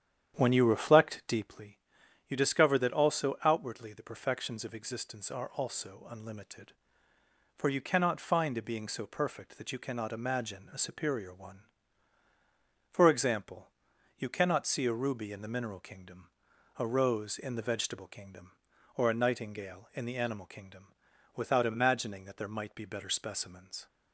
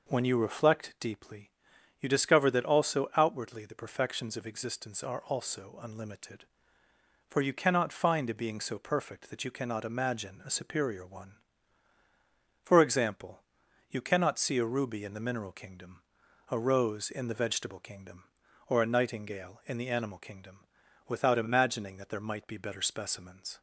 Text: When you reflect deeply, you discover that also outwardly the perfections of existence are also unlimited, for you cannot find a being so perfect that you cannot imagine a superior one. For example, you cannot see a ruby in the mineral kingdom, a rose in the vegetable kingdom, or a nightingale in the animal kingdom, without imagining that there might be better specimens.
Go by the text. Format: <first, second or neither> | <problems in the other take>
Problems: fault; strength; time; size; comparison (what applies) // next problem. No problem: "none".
second | starts louder than the rest; strong; until 1.6 s; 9.5 dB